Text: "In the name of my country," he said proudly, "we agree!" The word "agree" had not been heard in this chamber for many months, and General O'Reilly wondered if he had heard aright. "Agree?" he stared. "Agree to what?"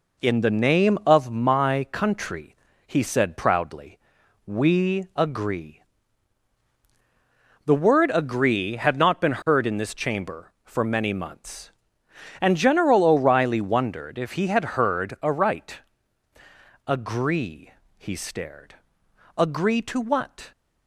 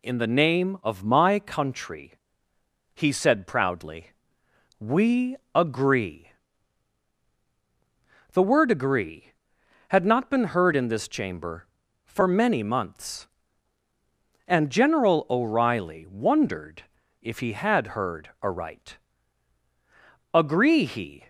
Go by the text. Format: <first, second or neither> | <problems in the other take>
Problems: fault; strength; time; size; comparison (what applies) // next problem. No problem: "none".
first | pauses between "we" and "agree"; slight; at 5.3 s; 0.18 s long // pauses between "wondered" and "if"; at 16.8 s; 0.38 s long // stops before "stared Agree to what"; at 21.2 s